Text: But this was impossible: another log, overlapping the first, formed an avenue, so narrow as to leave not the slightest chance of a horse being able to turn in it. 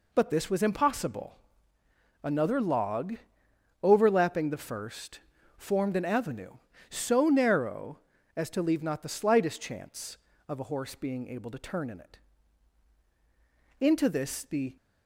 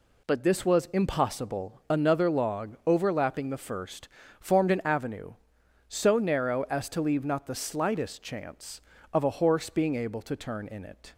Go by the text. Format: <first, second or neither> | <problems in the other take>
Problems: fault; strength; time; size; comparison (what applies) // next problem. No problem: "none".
second | goes on to say "Into this the"; noticeable; from 13.7 s on; 0.96 s long